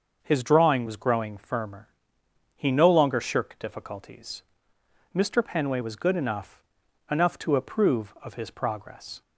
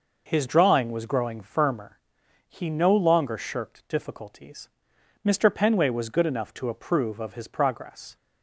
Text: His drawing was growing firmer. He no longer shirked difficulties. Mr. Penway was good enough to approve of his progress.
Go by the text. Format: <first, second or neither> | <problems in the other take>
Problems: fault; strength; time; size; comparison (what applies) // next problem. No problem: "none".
second | starts louder than the rest; until 1.2 s; 6 dB // says "enough" twice; at 7.0 s